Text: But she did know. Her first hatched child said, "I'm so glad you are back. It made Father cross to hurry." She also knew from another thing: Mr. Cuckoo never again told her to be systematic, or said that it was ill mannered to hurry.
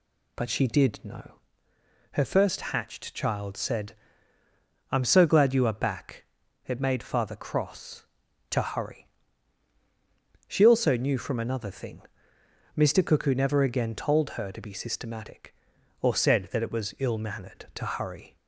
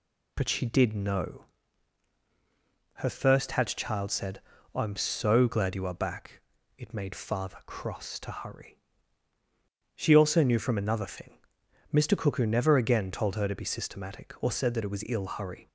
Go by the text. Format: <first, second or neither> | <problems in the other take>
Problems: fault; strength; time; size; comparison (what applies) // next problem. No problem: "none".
first | skips "mannered to"; at 15.2 s